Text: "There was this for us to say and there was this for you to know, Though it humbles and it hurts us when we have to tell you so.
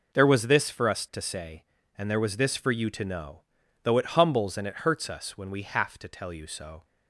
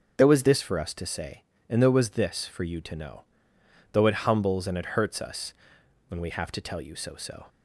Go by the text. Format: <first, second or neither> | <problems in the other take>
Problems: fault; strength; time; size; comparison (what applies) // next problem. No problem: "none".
first | starts louder than the rest; until 1.2 s; 6.5 dB // pauses between "us" and "when"; noticeable; at 5.5 s; 0.56 s long // says "so" twice; at 7.1 s